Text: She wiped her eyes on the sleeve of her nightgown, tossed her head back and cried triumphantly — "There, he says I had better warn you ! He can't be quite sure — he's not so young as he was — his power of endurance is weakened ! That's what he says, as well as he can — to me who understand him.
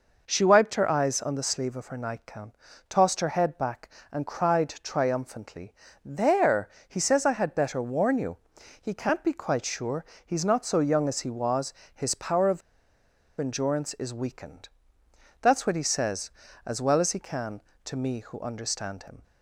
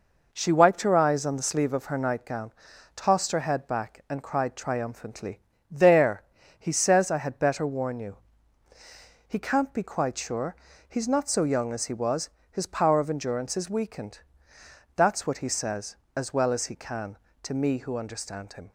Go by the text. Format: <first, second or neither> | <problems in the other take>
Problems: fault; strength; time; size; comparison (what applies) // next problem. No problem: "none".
second | pauses between "of" and "endurance"; noticeable; at 12.6 s; 0.79 s long